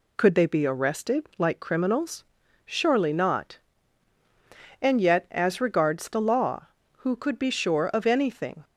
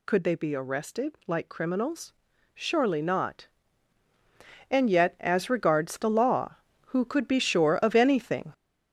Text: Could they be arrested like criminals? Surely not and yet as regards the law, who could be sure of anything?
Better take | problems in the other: first | gets louder; throughout; 6.5 dB

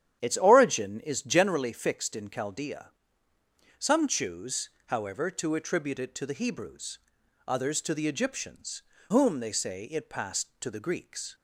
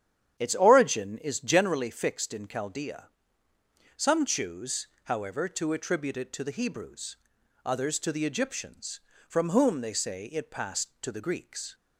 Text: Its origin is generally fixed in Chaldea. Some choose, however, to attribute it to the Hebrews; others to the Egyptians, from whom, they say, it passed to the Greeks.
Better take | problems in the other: second | starts louder than the rest; strong; until 1.2 s; 10 dB; strong in the second // skips "from"; at 8.9 s

